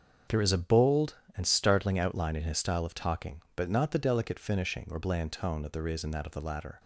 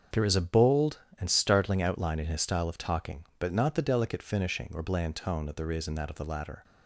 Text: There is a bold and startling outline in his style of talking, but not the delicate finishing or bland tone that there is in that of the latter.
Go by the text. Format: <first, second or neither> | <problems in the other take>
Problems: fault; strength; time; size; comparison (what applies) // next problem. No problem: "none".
neither | starts louder than the rest; the same in both